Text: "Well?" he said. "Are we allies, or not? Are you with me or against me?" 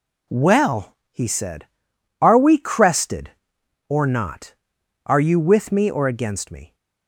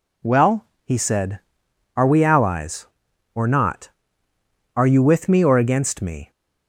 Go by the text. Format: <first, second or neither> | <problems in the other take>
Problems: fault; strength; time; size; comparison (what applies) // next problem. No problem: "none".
second | says "crested" for "allies"; at 2.5 s